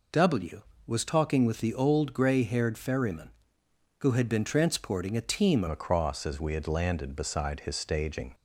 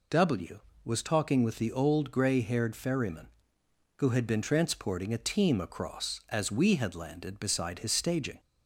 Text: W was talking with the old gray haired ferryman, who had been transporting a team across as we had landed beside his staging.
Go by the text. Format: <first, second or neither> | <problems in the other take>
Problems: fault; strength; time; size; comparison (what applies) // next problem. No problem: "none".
second | changes voice at "across"; from 5.6 s on; 2.7 s long